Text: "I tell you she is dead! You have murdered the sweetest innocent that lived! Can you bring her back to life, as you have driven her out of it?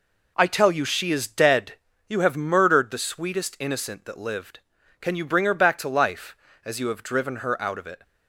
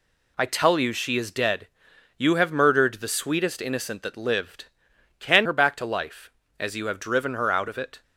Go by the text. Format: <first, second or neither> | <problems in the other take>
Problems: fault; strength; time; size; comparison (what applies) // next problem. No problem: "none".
first | skips "you bring"; at 5.4 s